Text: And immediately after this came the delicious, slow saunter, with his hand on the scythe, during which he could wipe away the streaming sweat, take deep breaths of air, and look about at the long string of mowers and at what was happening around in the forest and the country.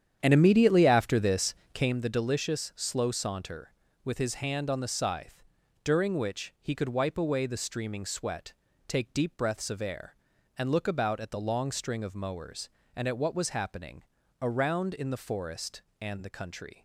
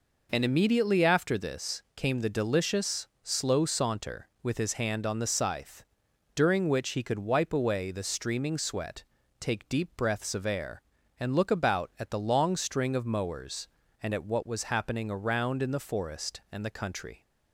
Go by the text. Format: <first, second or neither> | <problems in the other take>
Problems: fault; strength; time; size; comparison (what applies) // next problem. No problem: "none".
second | starts louder than the rest; strong; until 2.0 s; 9 dB // pauses between "this" and "came"; slight; at 1.5 s; 0.20 s long // pauses between "happening" and "around"; at 14.0 s; 0.38 s long